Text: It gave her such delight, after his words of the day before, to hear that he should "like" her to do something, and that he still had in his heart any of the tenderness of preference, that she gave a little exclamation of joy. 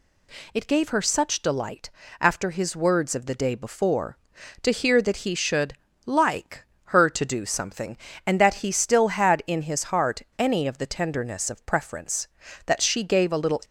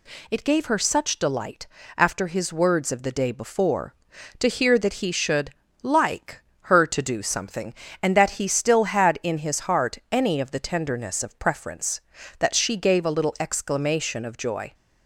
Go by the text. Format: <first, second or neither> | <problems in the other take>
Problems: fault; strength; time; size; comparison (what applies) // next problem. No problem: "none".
second | pauses between "should" and "like"; slight; at 5.7 s; 0.32 s long; slight in the second // pauses between "like" and "her"; slight; at 6.6 s; 0.22 s long; slight in the second // pauses between "heart" and "any"; slight; at 10.2 s; 0.17 s long // stops before "exclamation of joy"; at 13.6 s